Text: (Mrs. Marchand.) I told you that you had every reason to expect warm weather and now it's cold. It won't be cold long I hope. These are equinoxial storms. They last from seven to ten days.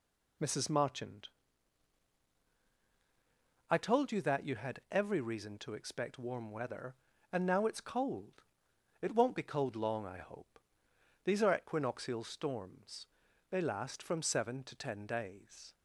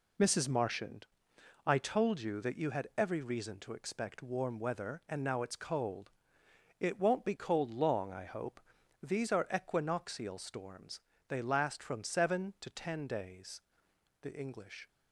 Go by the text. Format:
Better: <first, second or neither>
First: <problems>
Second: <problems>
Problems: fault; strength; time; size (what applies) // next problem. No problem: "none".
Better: first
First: none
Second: goes on to say "The English"; noticeable; from 14.2 s on; 0.66 s long